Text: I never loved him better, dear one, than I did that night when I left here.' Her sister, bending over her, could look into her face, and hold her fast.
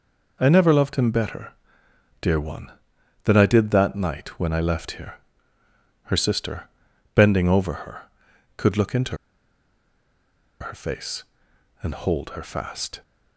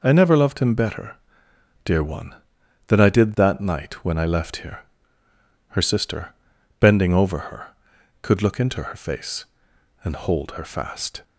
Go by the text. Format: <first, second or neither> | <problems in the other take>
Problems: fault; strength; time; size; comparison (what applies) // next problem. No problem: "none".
second | pauses between "into" and "her"; strong; at 9.1 s; 1.4 s long